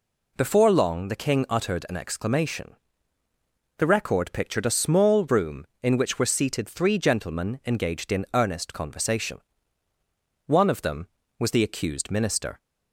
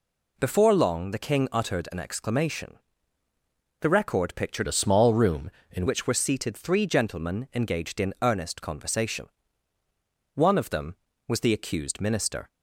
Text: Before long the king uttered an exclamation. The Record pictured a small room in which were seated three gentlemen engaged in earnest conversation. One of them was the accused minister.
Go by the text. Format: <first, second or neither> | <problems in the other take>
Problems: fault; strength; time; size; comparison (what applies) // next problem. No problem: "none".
first | changes voice from "a" to "in"; from 4.6 to 5.8 s; 1.2 s long